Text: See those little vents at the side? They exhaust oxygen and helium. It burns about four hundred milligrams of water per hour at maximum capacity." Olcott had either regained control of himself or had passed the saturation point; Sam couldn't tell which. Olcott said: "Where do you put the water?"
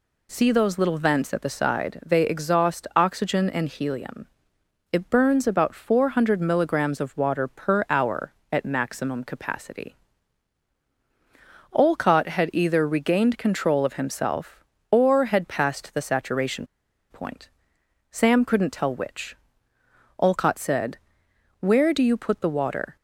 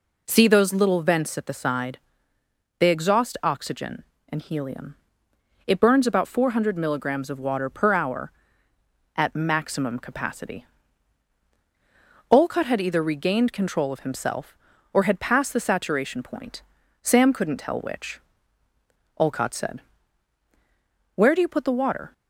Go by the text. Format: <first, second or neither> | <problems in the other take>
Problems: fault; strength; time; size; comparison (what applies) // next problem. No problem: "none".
second | pauses between "saturation" and "point"; noticeable; at 16.6 s; 0.46 s long